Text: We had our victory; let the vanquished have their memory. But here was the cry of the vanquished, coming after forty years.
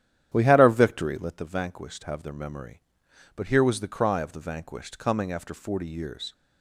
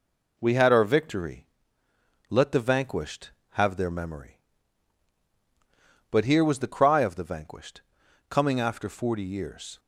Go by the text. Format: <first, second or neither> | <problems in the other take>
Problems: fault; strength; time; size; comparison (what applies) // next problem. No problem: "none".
second | starts louder than the rest; strong; until 1.4 s; 10.5 dB